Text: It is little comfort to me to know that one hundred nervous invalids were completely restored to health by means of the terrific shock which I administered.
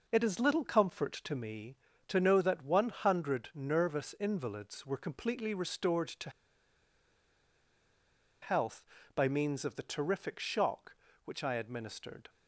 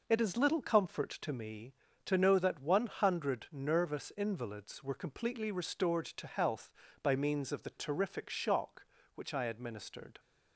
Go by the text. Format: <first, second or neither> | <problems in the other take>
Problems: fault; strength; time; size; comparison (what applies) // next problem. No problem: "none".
second | pauses between "to" and "health"; strong; at 6.2 s; 2.1 s long